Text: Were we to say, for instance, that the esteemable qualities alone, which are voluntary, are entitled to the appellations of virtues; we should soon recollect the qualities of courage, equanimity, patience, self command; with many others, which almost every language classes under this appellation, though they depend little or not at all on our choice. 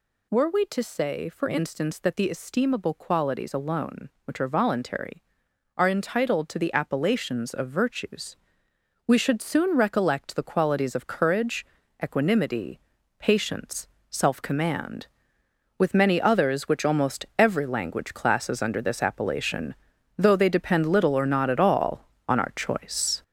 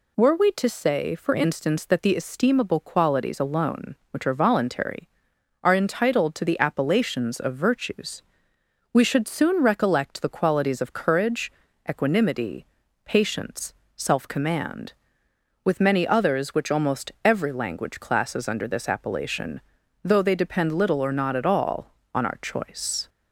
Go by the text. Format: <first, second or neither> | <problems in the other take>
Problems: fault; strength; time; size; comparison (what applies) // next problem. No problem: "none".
second | gets louder; throughout; 6.5 dB